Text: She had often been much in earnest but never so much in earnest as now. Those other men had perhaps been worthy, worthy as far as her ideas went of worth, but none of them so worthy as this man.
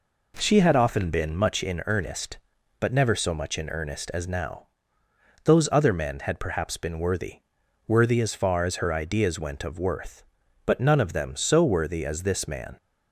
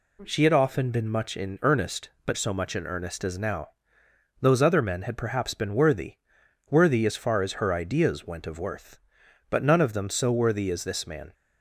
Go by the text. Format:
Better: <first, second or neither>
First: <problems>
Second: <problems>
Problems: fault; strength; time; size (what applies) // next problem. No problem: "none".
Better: first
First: none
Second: skips "never"; at 2.3 s